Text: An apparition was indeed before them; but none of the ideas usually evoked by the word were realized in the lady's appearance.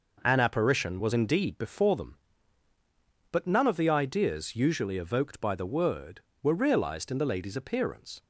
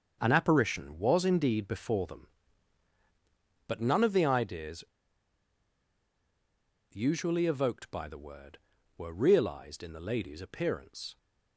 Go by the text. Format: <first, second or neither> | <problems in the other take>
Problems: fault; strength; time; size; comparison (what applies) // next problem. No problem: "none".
first | starts louder than the rest; until 1.2 s; 6.5 dB // pauses between "ideas" and "usually"; strong; at 4.8 s; 2.0 s long